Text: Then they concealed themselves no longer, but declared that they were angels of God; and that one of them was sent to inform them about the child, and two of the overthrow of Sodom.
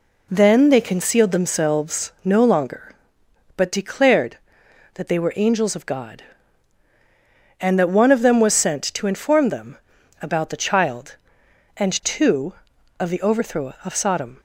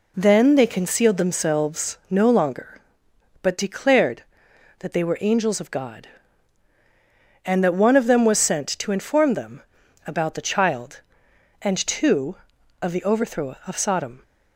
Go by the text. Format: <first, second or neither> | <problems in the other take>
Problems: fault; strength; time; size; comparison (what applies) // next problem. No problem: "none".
neither | pauses between "them" and "about"; the same in both